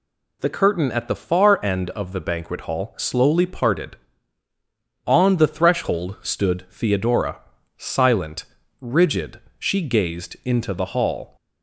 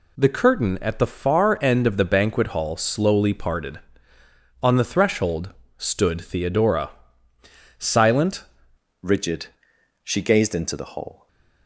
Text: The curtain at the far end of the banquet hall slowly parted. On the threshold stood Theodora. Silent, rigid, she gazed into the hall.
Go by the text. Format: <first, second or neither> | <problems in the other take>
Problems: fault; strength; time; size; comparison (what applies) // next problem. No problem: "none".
first | pauses between "threshold" and "stood"; slight; at 5.5 s; 0.24 s long // changes voice at "rigid"; from 9.0 s on; 2.2 s long // stays silent after the last word; slight; from 11.1 s on; 0.5 s long